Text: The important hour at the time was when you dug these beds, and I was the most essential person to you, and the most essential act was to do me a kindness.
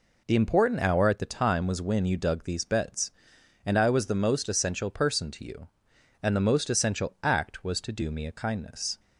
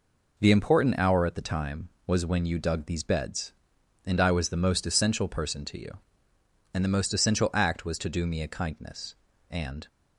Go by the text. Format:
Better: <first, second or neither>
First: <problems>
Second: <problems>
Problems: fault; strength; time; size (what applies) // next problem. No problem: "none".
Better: first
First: none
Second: goes on to say "And"; slight; from 9.4 s on; 0.38 s long